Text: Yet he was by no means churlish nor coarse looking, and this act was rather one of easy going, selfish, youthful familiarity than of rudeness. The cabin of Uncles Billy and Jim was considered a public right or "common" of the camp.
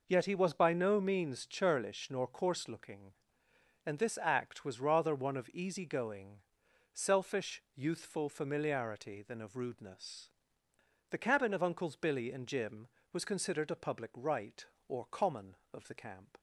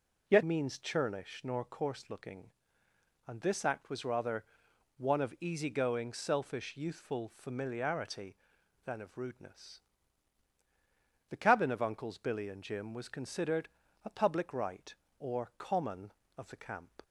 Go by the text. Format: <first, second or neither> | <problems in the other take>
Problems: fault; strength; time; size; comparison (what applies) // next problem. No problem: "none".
first | skips "he was by no"; at 0.4 s // pauses between "rather" and "one"; noticeable; at 4.4 s; 0.54 s long // pauses between "considered" and "a"; slight; at 13.6 s; 0.36 s long